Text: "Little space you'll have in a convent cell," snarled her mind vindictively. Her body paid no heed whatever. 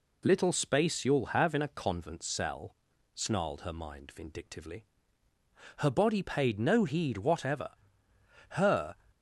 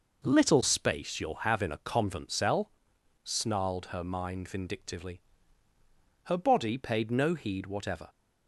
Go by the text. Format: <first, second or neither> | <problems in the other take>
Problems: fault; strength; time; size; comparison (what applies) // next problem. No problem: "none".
second | goes on to say "Her"; slight; from 8.5 s on; 0.44 s long